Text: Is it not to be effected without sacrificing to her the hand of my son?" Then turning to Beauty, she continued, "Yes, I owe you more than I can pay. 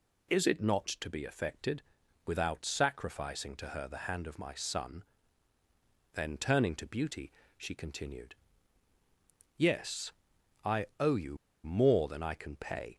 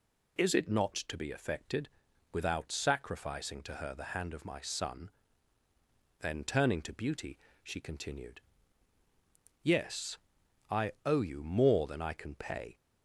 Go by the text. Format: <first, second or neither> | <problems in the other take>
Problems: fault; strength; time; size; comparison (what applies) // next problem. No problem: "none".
second | pauses between "effected" and "without"; noticeable; at 1.8 s; 0.46 s long; noticeable in the second // pauses between "you" and "more"; slight; at 11.3 s; 0.28 s long